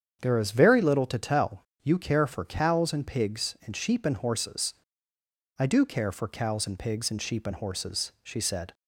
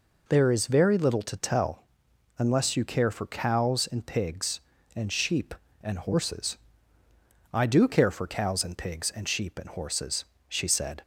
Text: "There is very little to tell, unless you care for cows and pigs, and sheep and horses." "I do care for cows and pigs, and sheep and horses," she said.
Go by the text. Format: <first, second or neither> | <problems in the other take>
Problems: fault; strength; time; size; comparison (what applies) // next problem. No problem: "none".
second | starts louder than the rest; strong; until 1.2 s; 8 dB // skips "unless"; at 1.7 s